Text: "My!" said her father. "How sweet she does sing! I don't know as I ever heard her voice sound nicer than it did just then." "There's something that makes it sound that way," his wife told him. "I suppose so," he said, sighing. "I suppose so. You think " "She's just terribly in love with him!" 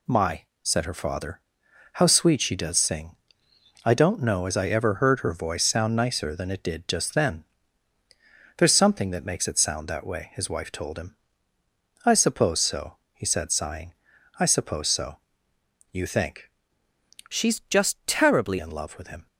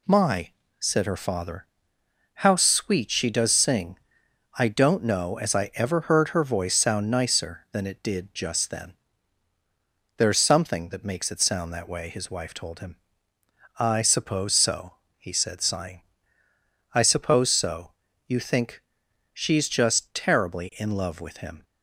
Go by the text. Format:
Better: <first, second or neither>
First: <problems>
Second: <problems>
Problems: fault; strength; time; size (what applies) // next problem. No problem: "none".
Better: second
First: changes voice from "She's" to "terribly"; from 17.2 to 18.5 s; 1.3 s long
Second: none